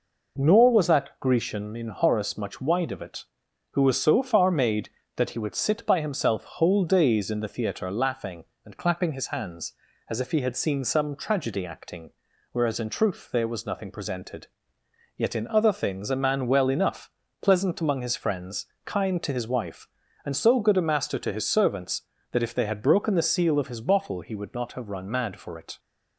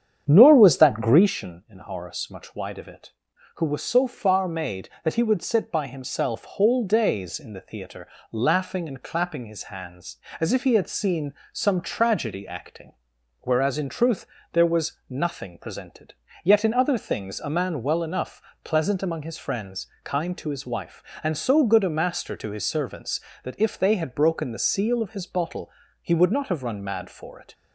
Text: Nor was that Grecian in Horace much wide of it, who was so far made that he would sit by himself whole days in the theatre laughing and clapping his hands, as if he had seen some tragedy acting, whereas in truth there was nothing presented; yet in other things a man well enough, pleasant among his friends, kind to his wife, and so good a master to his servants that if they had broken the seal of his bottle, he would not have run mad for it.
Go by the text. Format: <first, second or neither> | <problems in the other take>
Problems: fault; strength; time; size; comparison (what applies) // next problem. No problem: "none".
first | starts louder than the rest; strong; until 1.3 s; 8.5 dB // pauses between "theatre" and "laughing"; slight; at 8.0 s; 0.24 s long // pauses between "seen" and "some"; slight; at 11.3 s; 0.20 s long // pauses between "truth" and "there"; slight; at 14.2 s; 0.28 s long